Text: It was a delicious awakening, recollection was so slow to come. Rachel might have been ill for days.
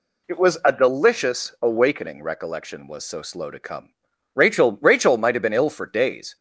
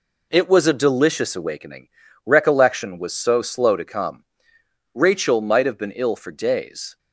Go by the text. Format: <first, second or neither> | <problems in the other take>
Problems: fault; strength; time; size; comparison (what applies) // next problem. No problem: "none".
second | says "Rachel" twice; at 4.7 s